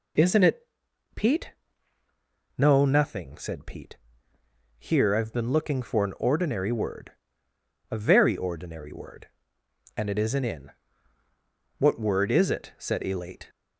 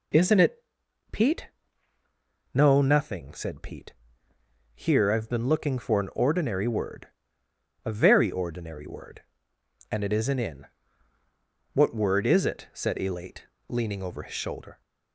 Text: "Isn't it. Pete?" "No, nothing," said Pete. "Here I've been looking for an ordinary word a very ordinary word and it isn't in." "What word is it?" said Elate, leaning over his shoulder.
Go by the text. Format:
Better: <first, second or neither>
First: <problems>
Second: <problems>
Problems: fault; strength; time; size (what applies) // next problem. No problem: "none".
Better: second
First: pauses between "word" and "a"; noticeable; at 7.1 s; 0.78 s long // stops before "leaning over his shoulder"; at 13.4 s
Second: pauses between "word" and "a"; noticeable; at 7.0 s; 0.76 s long